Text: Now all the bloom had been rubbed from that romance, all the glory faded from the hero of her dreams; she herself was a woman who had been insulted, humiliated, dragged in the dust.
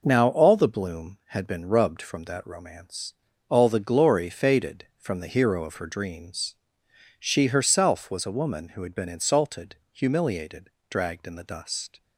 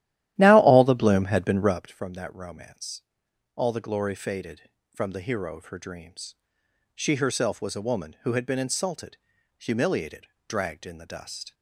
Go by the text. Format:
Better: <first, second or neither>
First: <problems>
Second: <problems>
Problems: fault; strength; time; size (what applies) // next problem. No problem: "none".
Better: first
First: none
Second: starts louder than the rest; strong; until 1.8 s; 13.5 dB